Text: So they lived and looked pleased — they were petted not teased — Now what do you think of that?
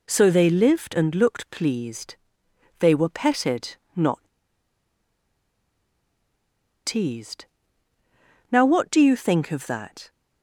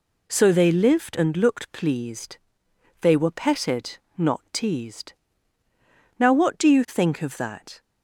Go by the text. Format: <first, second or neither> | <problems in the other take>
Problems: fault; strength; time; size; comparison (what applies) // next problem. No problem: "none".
second | pauses between "petted" and "not"; slight; at 3.7 s; 0.18 s long; slight in the second // pauses between "not" and "teased"; strong; at 4.1 s; 2.6 s long